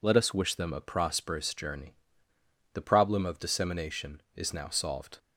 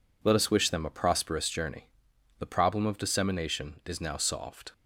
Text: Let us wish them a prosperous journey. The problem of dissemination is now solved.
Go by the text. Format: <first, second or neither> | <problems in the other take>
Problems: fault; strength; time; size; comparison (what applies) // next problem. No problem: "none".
neither | none